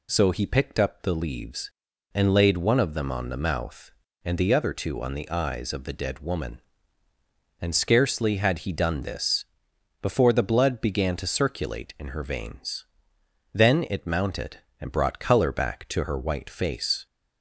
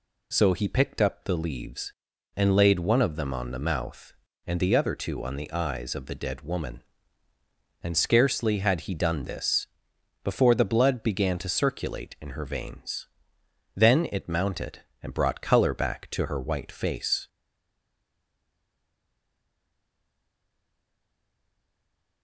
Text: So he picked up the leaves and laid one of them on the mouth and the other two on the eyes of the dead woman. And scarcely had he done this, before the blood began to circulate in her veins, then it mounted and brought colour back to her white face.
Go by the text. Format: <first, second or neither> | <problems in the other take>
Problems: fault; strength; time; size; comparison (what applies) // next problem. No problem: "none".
first | stays silent after the last word; strong; from 17.2 s on; 5.0 s long